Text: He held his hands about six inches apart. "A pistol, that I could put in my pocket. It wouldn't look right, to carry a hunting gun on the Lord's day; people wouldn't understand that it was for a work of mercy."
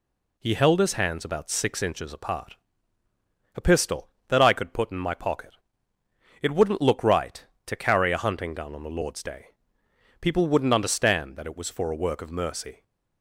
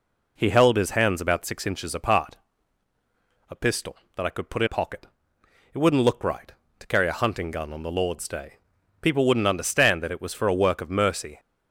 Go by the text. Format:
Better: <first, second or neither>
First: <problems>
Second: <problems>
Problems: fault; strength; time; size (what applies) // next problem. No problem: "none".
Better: first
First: none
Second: skips "my"; at 4.6 s